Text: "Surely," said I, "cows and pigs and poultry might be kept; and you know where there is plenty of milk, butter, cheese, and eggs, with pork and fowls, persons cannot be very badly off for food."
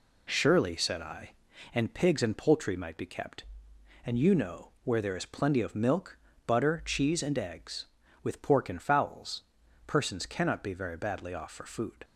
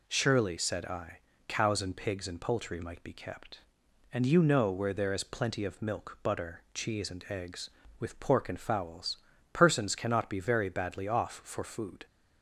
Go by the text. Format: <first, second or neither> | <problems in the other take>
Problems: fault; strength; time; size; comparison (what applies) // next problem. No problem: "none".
second | skips "cows"; at 1.5 s